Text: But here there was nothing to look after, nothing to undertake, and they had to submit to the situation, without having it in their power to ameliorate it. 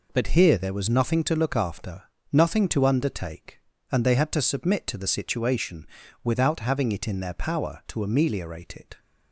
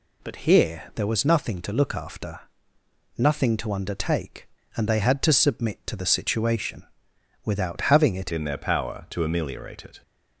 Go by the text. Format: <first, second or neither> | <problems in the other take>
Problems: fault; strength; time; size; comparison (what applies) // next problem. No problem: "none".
first | changes voice at "in"; from 8.3 s on; 1.7 s long